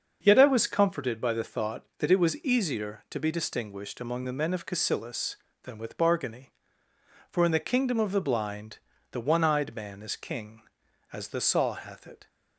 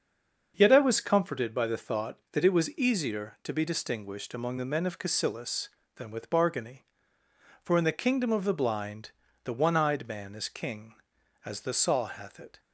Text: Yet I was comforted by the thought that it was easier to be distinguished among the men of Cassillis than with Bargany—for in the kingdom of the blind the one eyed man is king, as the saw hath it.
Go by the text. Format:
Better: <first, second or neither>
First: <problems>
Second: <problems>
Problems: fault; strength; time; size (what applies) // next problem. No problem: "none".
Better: first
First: starts louder than the rest; until 1.2 s; 6.5 dB // pauses between "blind" and "the"; slight; at 8.7 s; 0.36 s long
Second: stays silent before the first word; slight; until 0.5 s; 0.5 s long // starts louder than the rest; until 1.5 s; 6.5 dB // pauses between "blind" and "the"; slight; at 9.0 s; 0.36 s long